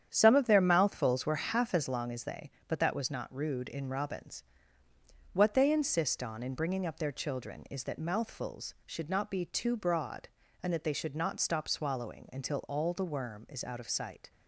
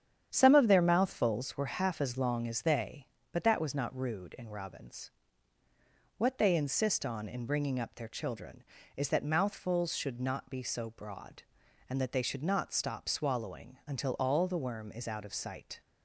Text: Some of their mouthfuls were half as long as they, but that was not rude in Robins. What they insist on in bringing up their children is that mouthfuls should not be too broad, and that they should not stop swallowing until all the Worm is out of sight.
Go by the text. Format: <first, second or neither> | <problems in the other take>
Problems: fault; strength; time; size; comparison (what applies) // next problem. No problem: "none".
first | starts louder than the rest; strong; until 1.3 s; 9 dB; strong in the first // says "so" for "too"; at 10.6 s